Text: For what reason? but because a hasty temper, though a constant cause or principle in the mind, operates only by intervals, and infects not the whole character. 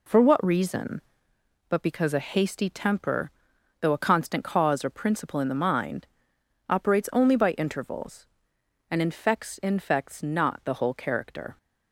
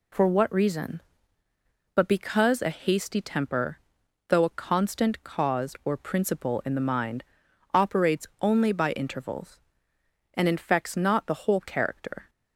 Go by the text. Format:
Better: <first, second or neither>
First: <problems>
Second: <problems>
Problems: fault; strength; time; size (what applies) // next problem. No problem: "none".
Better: second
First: says "infects" twice; at 9.5 s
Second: none